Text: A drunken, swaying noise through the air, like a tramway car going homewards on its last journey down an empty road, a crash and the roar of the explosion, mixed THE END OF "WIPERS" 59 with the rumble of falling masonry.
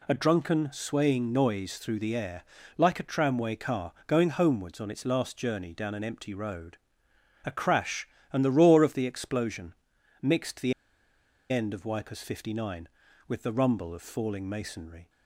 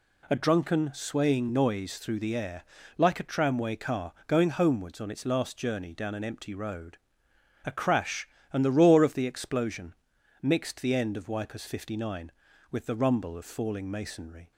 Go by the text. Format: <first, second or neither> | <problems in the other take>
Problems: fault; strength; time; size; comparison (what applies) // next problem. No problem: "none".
second | pauses between "car" and "going"; slight; at 3.9 s; 0.16 s long; slight in the second // pauses between "THE" and "END"; noticeable; at 10.7 s; 0.78 s long